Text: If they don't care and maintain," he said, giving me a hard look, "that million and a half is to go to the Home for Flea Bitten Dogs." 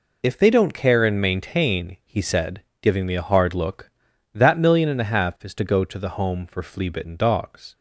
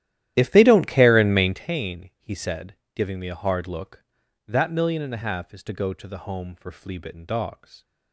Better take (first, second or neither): first